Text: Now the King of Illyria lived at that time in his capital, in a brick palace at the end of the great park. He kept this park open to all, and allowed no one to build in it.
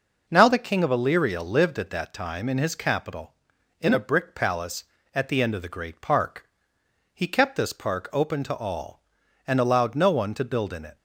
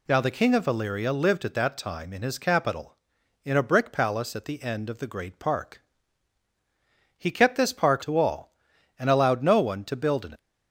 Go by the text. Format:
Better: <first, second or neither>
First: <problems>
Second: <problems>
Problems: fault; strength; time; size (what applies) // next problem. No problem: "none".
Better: first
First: none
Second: skips "open"; at 8.0 s